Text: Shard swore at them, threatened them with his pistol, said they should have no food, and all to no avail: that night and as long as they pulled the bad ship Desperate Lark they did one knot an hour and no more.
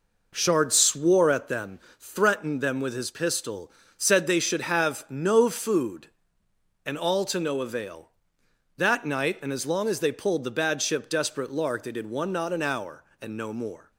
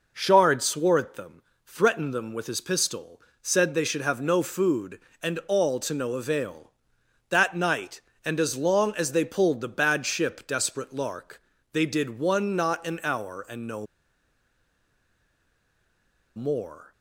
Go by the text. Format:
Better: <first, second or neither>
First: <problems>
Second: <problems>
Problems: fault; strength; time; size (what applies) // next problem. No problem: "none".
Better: first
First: none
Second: pauses between "Lark" and "they"; slight; at 11.4 s; 0.30 s long // pauses between "no" and "more"; strong; at 13.8 s; 2.5 s long